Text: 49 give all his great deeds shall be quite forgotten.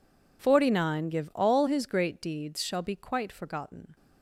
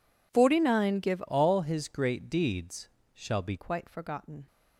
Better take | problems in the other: first | changes voice from "all" to "be"; from 1.2 to 3.5 s; 2.3 s long // pauses between "deeds" and "shall"; slight; at 2.8 s; 0.28 s long

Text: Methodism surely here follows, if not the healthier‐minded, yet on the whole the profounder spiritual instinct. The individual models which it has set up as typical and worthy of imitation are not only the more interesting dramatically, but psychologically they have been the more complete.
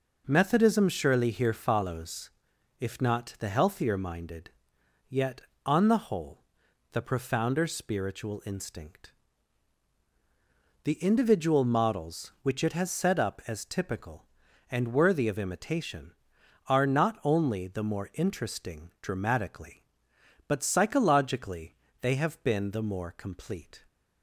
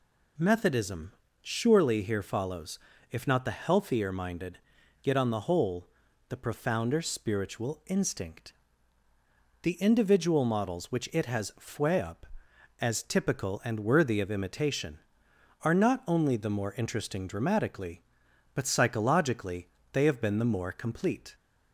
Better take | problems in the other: first | pauses between "Methodism" and "surely"; slight; at 1.1 s; 0.30 s long // pauses between "whole" and "the"; at 5.8 s; 0.40 s long; noticeable in the first // says "fue" for "set"; at 11.5 s // pauses between "psychologically" and "they"; slight; at 19.6 s; 0.26 s long; slight in the first

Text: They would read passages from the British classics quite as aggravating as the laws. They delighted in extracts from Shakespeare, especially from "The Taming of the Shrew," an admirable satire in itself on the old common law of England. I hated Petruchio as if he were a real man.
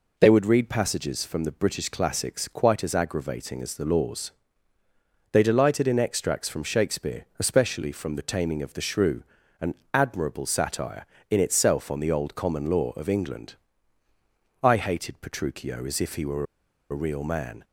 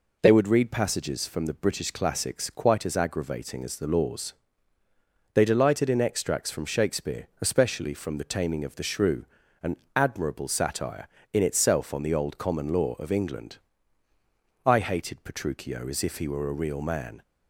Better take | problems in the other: second | pauses between "an" and "admirable"; slight; at 9.7 s; 0.18 s long; slight in the second // pauses between "were" and "a"; noticeable; at 16.4 s; 0.46 s long

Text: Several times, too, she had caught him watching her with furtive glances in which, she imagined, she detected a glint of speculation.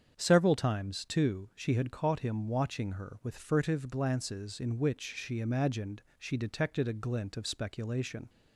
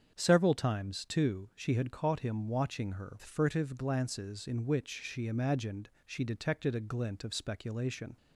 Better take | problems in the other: first | starts louder than the rest; strong; until 1.1 s; 7.5 dB; strong in the first // skips "with"; at 3.1 s

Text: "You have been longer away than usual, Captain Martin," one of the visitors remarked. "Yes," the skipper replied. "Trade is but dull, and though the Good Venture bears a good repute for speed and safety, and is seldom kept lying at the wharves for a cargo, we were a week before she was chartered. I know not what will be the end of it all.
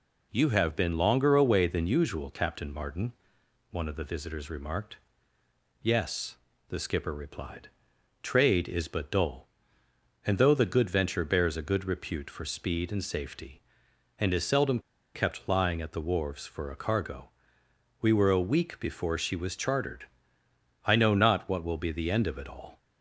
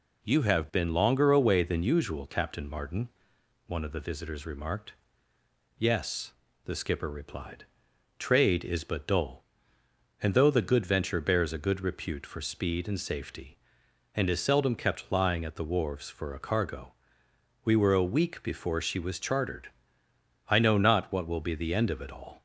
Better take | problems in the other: second | pauses between "seldom" and "kept"; slight; at 14.7 s; 0.35 s long

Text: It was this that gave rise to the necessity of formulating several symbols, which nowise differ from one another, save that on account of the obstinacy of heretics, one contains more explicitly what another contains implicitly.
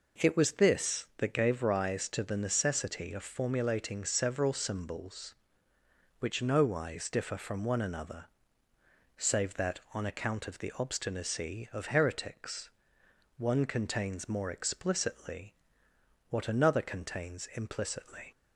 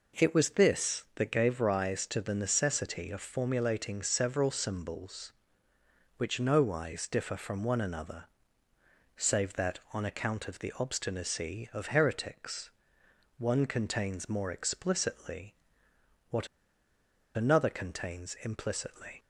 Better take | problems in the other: first | pauses between "explicitly" and "what"; noticeable; at 15.5 s; 0.74 s long; noticeable in the first // pauses between "what" and "another"; noticeable; at 16.4 s; 0.88 s long

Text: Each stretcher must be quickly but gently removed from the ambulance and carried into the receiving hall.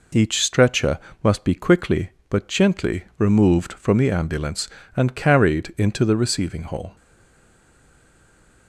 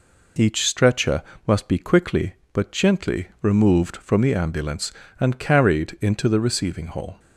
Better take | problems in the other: second | pauses between "stretcher" and "must"; slight; at 0.9 s; 0.24 s long; slight in the second // stays silent after the last word; noticeable; from 6.9 s on; 1.7 s long

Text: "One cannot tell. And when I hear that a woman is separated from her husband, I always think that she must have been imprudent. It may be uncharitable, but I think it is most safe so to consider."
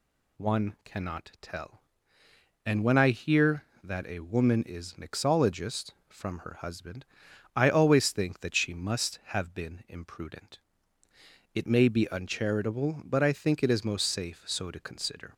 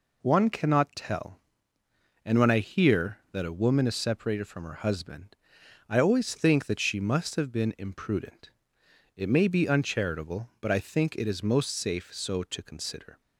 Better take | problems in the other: second | says "mixologist" for "separated"; at 4.9 s

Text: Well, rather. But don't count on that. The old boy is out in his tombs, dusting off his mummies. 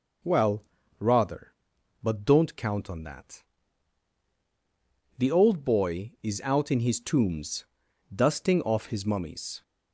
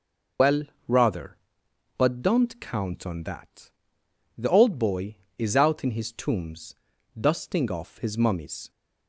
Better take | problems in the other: first | loses the start of "Well"; at 0.3 s; 100 ms

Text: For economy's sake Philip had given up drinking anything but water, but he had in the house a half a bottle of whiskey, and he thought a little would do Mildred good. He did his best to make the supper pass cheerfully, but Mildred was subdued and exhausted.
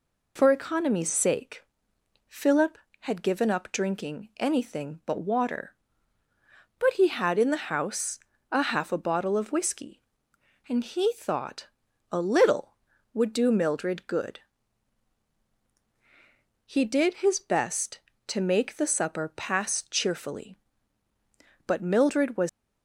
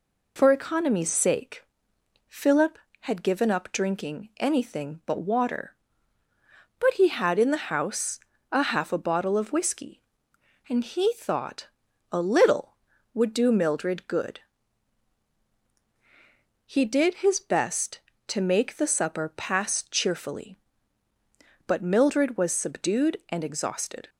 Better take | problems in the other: second | pauses between "sake" and "Philip"; noticeable; at 1.6 s; 0.64 s long; noticeable in the second // pauses between "house" and "a"; slight; at 8.1 s; 0.32 s long; slight in the second // pauses between "thought" and "a"; at 11.6 s; 0.42 s long; also in the second // stops before "subdued and exhausted"; at 22.4 s

